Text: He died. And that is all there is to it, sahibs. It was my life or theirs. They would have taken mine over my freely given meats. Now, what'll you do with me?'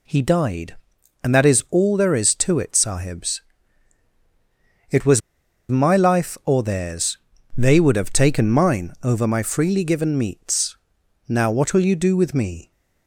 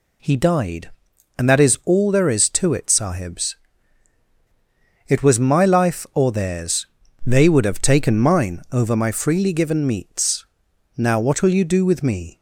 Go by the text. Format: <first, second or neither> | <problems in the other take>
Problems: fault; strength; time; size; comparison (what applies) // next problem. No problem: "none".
second | pauses between "was" and "my"; noticeable; at 5.2 s; 0.48 s long